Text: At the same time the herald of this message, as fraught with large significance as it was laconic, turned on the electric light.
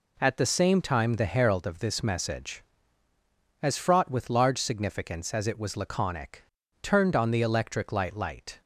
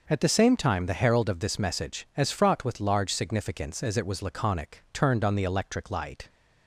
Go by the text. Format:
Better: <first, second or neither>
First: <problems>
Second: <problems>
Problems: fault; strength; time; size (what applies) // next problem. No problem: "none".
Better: second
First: says "light" twice; at 8.1 s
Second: none